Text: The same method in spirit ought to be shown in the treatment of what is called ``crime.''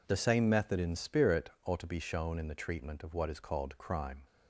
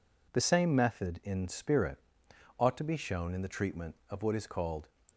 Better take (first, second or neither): first